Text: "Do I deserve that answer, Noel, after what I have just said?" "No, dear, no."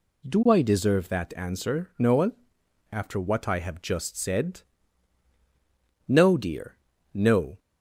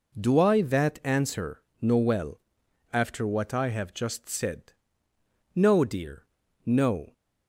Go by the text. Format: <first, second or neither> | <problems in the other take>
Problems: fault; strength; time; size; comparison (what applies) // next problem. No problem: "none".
first | skips "deserve"; at 0.6 s